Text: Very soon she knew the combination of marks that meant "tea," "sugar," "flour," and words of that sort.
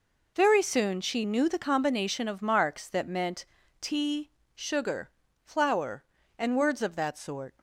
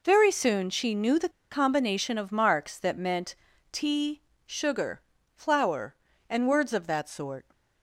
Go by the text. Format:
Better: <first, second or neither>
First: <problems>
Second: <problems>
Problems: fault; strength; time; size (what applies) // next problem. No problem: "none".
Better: first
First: pauses between "meant" and "tea"; slight; at 3.4 s; 0.34 s long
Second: pauses between "the" and "combination"; slight; at 1.2 s; 0.22 s long // pauses between "meant" and "tea"; slight; at 3.3 s; 0.36 s long